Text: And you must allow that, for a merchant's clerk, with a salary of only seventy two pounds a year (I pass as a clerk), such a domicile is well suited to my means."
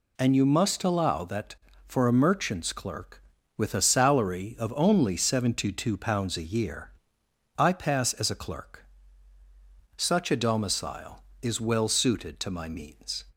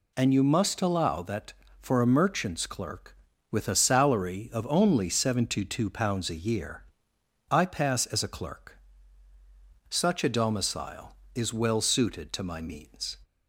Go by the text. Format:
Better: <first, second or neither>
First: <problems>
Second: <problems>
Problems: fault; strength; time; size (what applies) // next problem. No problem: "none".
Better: neither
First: none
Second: none